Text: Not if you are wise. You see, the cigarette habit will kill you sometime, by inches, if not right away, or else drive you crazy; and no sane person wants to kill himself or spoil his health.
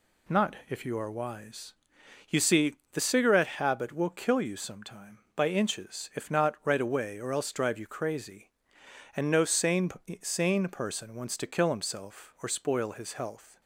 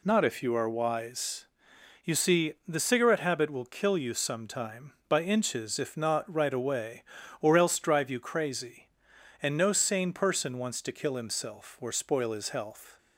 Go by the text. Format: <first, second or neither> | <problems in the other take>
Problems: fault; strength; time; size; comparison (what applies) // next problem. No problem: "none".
second | says "sane" twice; at 10.2 s